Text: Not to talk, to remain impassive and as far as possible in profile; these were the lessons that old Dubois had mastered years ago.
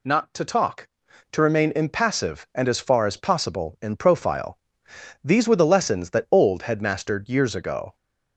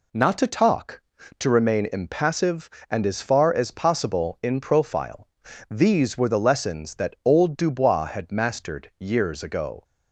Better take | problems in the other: second | skips "Dubois"; at 6.6 s

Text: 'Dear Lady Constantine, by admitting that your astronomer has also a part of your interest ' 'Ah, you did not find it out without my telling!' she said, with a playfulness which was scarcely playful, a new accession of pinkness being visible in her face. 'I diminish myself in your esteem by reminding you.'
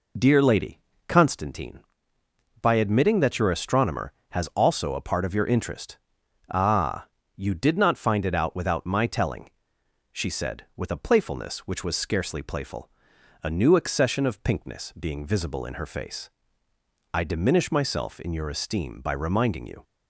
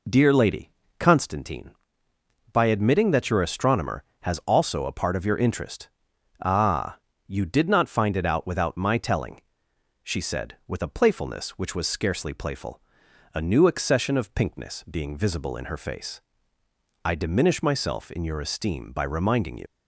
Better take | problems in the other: first | pauses between "Lady" and "Constantine"; slight; at 0.6 s; 0.30 s long; slight in the first // leaves "you" unfinished; at 19.6 s; 80 ms

